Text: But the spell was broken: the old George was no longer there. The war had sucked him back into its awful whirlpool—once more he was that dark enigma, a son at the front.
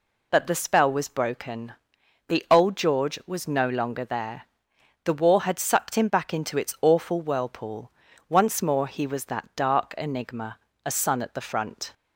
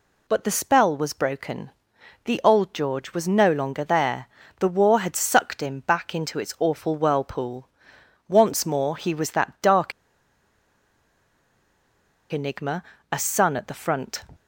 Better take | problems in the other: first | pauses between "dark" and "enigma"; strong; at 9.9 s; 2.4 s long

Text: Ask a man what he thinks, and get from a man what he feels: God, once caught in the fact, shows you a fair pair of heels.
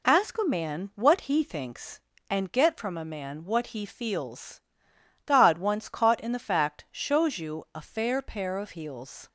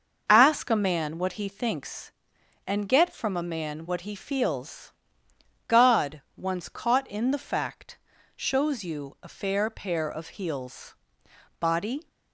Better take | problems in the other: first | starts louder than the rest; until 1.2 s; 6 dB // goes on to say "Body"; slight; from 11.5 s on; 0.48 s long

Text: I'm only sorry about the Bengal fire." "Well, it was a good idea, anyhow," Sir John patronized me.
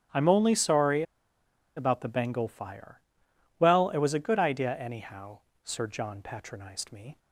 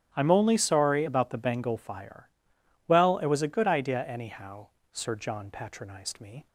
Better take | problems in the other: second | starts louder than the rest; strong; until 1.8 s; 9.5 dB; strong in the second // pauses between "sorry" and "about"; noticeable; at 1.0 s; 0.73 s long

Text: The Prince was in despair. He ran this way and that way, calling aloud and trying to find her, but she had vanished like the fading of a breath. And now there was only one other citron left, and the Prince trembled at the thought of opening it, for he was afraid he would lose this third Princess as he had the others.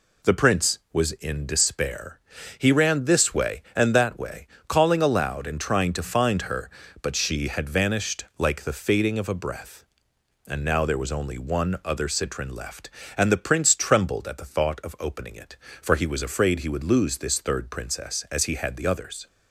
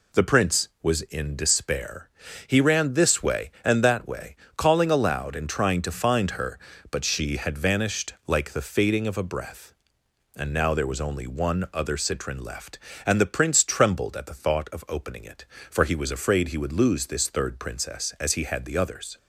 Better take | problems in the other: neither | none

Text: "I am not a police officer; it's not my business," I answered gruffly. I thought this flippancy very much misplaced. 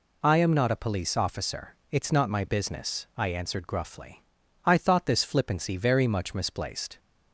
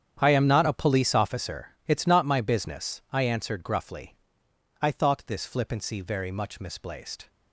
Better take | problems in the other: first | gets quieter; strong; throughout; 14.5 dB

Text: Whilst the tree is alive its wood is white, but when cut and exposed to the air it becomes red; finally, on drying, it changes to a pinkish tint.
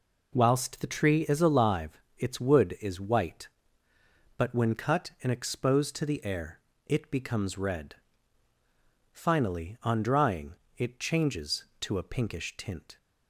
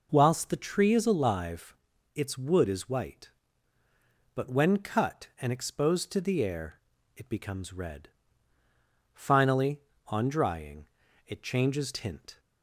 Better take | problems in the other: first | pauses between "alive" and "its"; at 1.7 s; 0.42 s long; slight in the first // pauses between "air" and "it"; slight; at 6.8 s; 0.34 s long; slight in the first // skips "to a pinkish"; at 11.9 s

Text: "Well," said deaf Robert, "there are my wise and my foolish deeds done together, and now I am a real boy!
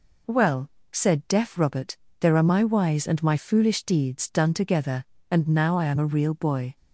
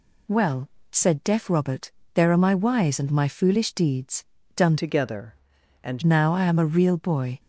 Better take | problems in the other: first | pauses between "deeds" and "done"; slight; at 4.2 s; 0.32 s long // changes voice from "together" to "and"; from 4.7 to 6.0 s; 1.3 s long

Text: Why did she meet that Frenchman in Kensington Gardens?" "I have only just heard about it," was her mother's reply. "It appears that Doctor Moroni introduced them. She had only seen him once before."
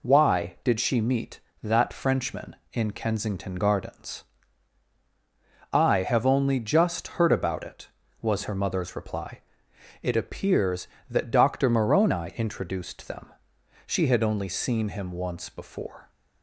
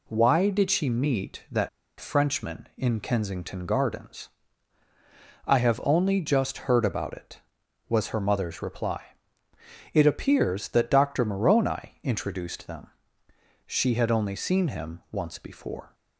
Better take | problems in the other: first | pauses between "that" and "Frenchman"; slight; at 1.6 s; 0.30 s long

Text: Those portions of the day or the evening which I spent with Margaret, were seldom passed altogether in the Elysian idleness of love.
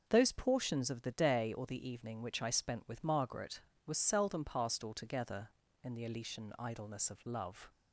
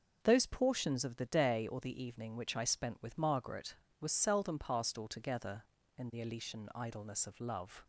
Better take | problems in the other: neither | none

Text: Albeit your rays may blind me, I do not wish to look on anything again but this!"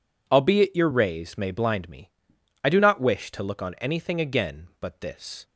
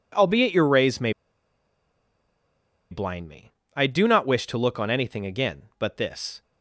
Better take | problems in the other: first | pauses between "may" and "blind"; strong; at 1.1 s; 1.7 s long

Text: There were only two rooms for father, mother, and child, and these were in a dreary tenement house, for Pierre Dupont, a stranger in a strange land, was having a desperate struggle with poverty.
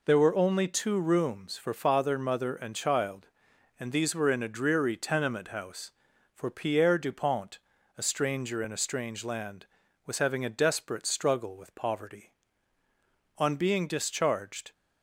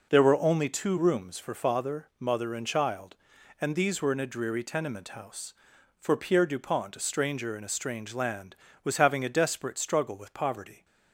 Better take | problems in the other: second | goes on to say "On being discharged"; from 13.3 s on; 1.3 s long

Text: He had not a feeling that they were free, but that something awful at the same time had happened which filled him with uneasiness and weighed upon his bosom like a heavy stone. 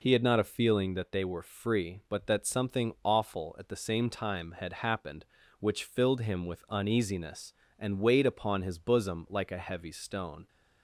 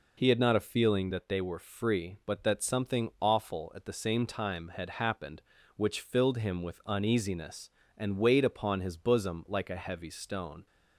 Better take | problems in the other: neither | none

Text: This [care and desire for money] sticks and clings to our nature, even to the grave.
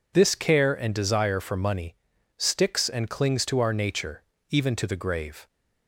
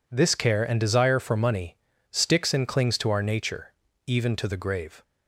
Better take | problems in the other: neither | pauses between "money" and "sticks"; the same in both

